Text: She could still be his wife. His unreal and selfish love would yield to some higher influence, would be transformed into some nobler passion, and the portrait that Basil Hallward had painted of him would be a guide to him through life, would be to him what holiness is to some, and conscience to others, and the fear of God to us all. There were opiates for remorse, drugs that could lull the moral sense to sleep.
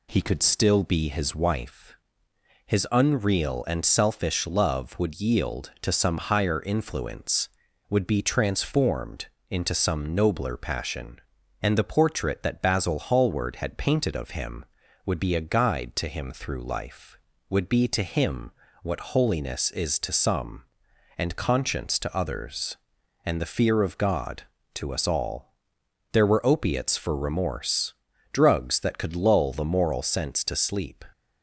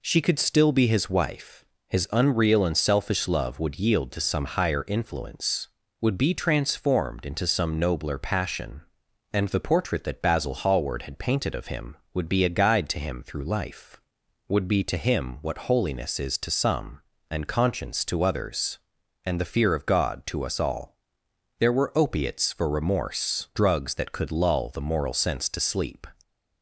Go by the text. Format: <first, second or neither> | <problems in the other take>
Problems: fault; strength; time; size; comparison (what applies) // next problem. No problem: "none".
second | says "He" for "She"; at 0.0 s // pauses between "transformed" and "into"; slight; at 9.2 s; 0.24 s long // pauses between "him" and "what"; slight; at 18.4 s; 0.32 s long